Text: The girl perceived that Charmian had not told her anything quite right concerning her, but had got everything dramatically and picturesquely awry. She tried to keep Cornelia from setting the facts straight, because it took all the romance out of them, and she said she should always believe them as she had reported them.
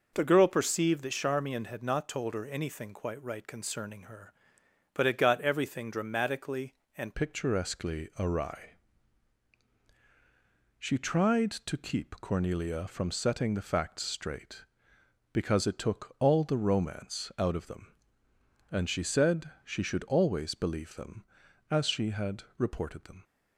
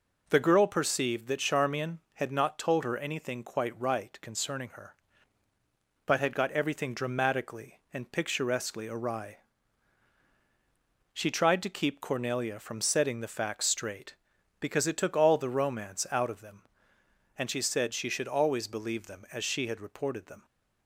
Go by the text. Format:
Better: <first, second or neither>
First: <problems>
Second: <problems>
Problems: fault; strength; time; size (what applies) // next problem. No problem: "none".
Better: second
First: changes voice at "picturesquely"; from 7.1 s on; 16.1 s long // pauses between "said" and "she"; slight; at 19.4 s; 0.16 s long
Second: none